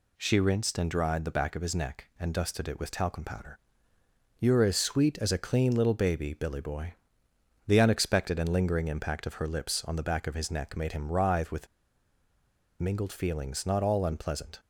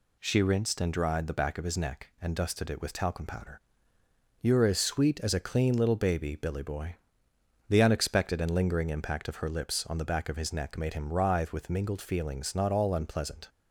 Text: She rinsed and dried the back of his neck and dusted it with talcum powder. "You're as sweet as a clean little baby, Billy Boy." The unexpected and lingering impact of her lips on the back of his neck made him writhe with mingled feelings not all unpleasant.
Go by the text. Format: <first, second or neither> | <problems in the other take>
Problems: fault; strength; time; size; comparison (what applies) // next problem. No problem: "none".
second | pauses between "with" and "mingled"; at 11.6 s; 1.1 s long